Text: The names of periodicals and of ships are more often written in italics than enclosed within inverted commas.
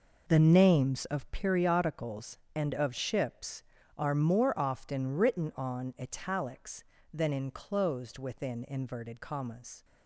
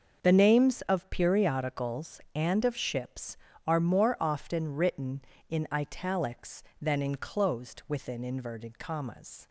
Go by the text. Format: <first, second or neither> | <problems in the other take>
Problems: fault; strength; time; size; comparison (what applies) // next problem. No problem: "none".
second | says "on" for "in"; at 5.5 s